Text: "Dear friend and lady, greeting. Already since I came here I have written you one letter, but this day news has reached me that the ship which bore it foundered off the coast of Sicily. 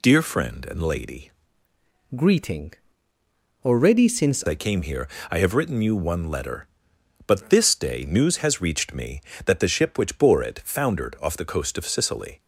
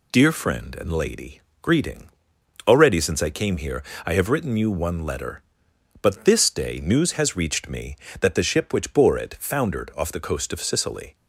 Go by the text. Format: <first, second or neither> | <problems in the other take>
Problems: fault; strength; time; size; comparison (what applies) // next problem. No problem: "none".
second | changes voice from "greeting" to "since"; from 2.1 to 4.4 s; 2.3 s long // pauses between "here" and "I"; slight; at 5.0 s; 0.22 s long; slight in the second